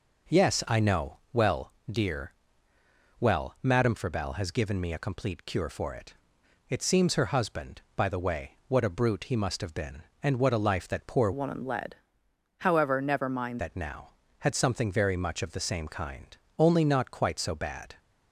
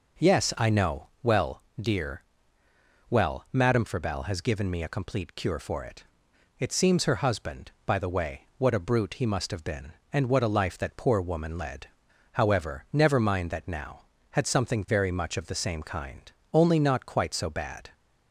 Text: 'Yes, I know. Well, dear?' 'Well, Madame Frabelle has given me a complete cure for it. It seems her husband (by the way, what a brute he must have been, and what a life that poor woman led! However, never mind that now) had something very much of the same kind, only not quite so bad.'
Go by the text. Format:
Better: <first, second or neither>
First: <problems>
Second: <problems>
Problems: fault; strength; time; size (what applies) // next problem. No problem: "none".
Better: second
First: changes voice from "woman" to "mind"; from 11.3 to 13.5 s; 2.2 s long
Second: none